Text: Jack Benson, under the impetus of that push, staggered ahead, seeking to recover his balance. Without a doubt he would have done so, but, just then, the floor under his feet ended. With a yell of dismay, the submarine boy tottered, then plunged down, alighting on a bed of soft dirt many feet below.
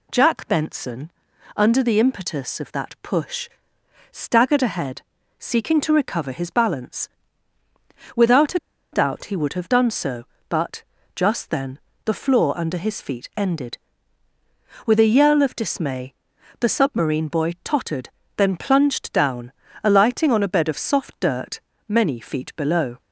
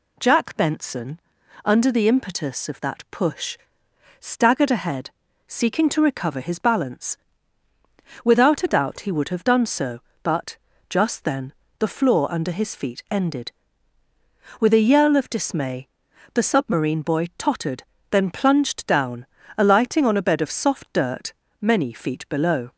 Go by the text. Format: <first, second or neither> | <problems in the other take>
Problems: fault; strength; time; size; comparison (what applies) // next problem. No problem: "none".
second | pauses between "a" and "doubt"; slight; at 8.5 s; 0.33 s long // pauses between "dirt" and "many"; slight; at 21.6 s; 0.26 s long; slight in the second